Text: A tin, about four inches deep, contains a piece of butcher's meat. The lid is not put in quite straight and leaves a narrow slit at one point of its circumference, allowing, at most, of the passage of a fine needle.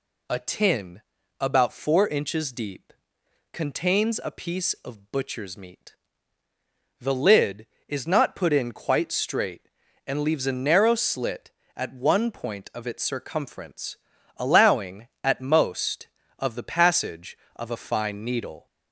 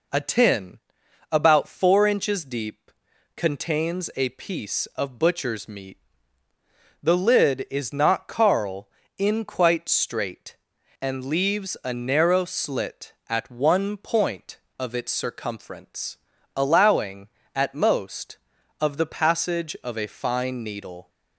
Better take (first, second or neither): first